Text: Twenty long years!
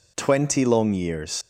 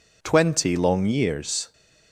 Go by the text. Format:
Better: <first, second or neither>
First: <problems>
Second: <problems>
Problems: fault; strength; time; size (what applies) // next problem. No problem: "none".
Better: second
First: leaves "years" unfinished; at 1.4 s; 120 ms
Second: none